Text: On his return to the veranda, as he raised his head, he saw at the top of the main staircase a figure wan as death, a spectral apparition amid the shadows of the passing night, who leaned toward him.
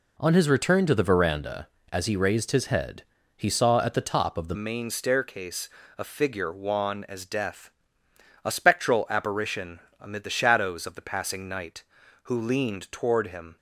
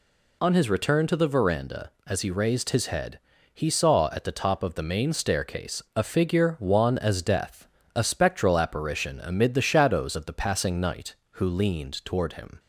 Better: second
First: changes voice at "main"; from 4.5 s on; 9.0 s long // pauses between "staircase" and "a"; slight; at 5.6 s; 0.30 s long // pauses between "apparition" and "amid"; slight; at 9.7 s; 0.20 s long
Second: none

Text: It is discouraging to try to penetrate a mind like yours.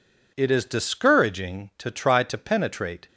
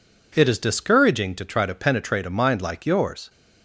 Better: second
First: stops before "a mind like yours"; at 3.0 s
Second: none

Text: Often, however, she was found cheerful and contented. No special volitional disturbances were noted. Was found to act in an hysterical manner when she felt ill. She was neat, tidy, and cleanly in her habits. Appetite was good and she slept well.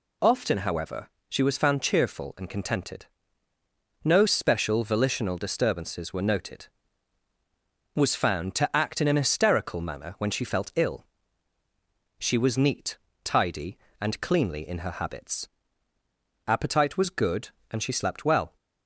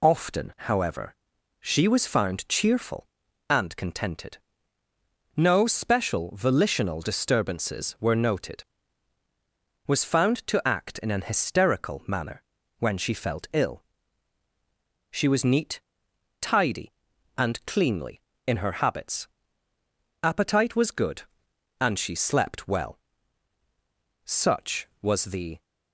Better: first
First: none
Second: pauses between "manner" and "when"; at 12.4 s; 0.38 s long // goes on to say "Such was the"; from 24.2 s on; 1.3 s long

